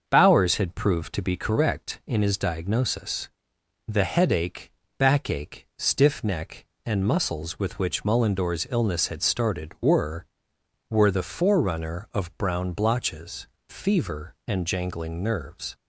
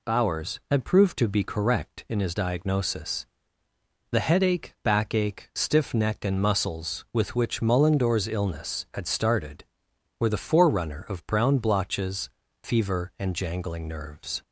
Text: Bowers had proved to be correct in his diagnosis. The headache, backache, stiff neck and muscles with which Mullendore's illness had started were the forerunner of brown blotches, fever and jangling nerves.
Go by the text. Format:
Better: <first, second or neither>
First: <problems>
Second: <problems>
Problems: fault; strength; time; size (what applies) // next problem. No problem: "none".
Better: second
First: starts louder than the rest; until 1.0 s; 6.5 dB // says "were" twice; at 10.9 s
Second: none